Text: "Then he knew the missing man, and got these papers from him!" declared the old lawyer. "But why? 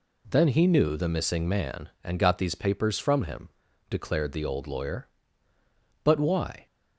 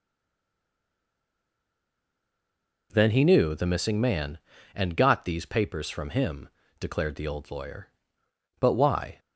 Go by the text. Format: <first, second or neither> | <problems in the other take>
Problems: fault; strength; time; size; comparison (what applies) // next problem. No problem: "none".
first | stays silent before the first word; strong; until 2.9 s; 2.9 s long